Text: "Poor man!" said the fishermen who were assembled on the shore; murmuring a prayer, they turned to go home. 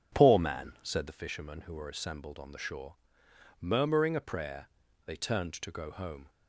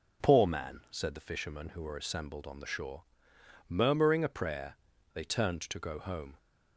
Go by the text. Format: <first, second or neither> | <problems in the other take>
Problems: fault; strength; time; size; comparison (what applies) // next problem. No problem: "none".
second | starts louder than the rest; strong; until 1.2 s; 8 dB